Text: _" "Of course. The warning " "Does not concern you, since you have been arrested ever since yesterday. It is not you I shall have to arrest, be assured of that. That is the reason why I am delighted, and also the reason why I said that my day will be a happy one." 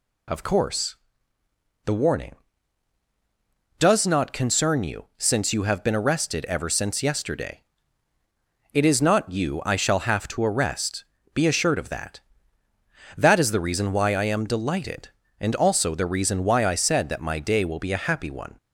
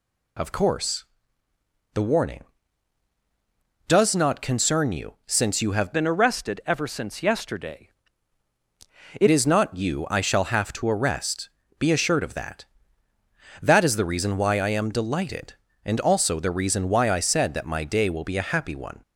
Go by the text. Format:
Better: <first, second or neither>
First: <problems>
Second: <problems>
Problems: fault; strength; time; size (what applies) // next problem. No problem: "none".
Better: first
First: none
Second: changes voice from "been" to "It"; from 5.9 to 9.2 s; 3.3 s long